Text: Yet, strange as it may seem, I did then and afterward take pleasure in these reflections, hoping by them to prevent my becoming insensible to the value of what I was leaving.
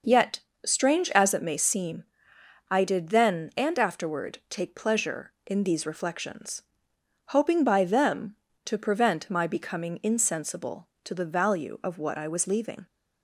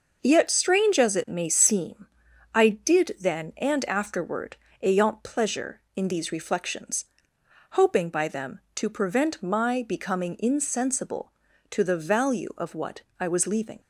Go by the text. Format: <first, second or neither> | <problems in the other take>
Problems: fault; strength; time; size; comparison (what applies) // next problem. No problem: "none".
first | says "ayant" for "take"; at 4.8 s // pauses between "what" and "I"; slight; at 13.0 s; 0.16 s long